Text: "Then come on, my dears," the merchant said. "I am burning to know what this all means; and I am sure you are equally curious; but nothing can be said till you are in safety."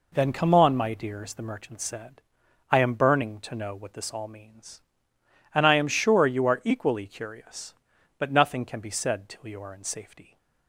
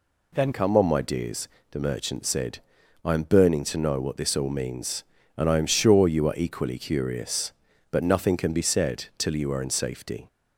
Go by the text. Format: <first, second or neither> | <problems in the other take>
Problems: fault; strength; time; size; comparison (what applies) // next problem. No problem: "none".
first | changes voice at "come"; from 0.5 s on; 9.7 s long